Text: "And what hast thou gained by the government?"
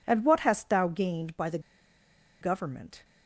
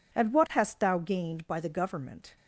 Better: second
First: pauses between "the" and "government"; noticeable; at 1.5 s; 0.82 s long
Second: none

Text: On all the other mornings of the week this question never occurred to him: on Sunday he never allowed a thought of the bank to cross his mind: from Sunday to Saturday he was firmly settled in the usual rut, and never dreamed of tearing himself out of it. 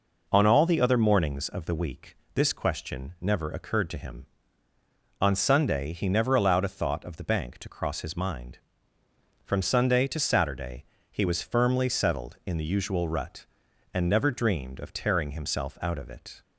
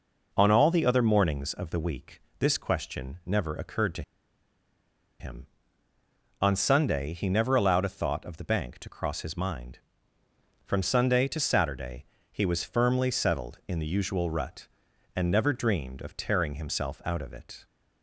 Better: first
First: pauses between "week" and "this"; slight; at 2.1 s; 0.18 s long // pauses between "Saturday" and "he"; slight; at 10.8 s; 0.30 s long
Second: pauses between "week" and "this"; slight; at 2.2 s; 0.18 s long // pauses between "to" and "him"; at 4.0 s; 1.1 s long // pauses between "Saturday" and "he"; slight; at 12.0 s; 0.30 s long

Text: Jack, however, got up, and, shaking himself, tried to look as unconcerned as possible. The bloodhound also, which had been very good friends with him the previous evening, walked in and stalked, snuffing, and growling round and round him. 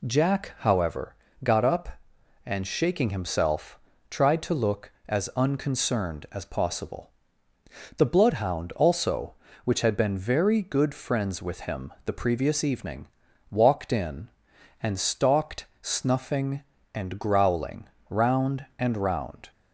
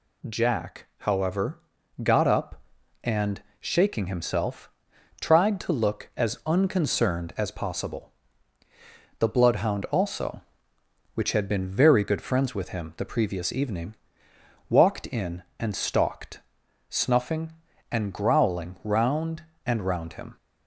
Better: second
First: pauses between "growling" and "round"; slight; at 17.8 s; 0.20 s long // stops before "him"; at 19.5 s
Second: none

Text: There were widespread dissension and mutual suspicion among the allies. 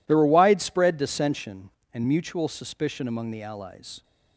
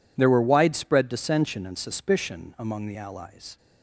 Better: first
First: none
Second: skips "mutual"; at 1.7 s

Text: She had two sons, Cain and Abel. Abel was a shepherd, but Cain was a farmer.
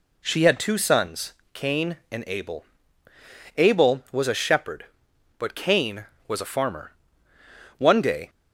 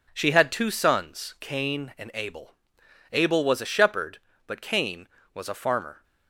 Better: second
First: goes on to say "One day"; from 7.7 s on; 0.52 s long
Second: none

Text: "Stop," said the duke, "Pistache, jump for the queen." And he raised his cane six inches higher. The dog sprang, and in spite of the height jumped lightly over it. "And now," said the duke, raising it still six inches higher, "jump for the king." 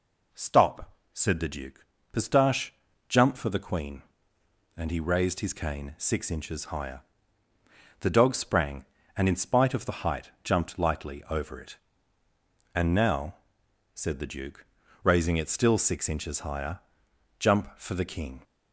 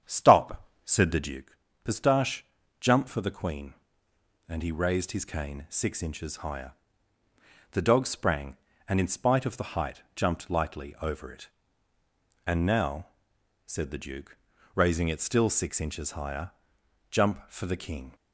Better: first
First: none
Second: starts louder than the rest; strong; until 1.4 s; 8.5 dB

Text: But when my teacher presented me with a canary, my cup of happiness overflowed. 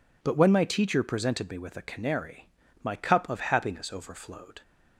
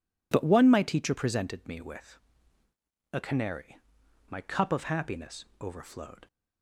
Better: first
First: none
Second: says "one" for "when"; at 0.4 s // pauses between "with" and "a"; noticeable; at 2.1 s; 0.96 s long

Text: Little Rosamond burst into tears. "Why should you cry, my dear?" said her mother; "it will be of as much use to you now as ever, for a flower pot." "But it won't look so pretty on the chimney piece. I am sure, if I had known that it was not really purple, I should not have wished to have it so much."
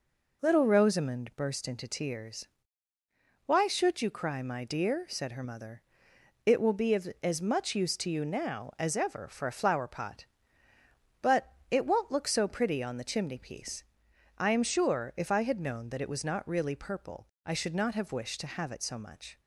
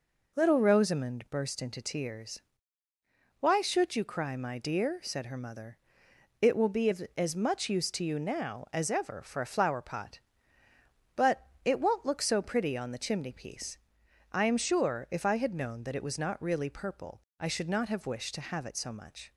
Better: neither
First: pauses between "But" and "it"; slight; at 11.5 s; 0.20 s long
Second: pauses between "But" and "it"; slight; at 11.4 s; 0.20 s long

